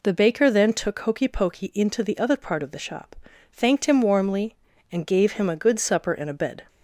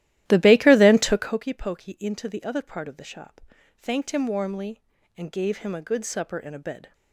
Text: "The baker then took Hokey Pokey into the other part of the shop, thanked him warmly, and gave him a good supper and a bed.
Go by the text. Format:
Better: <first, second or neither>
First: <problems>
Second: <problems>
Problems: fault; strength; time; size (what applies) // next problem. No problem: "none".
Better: first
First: none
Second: starts louder than the rest; strong; until 1.4 s; 14 dB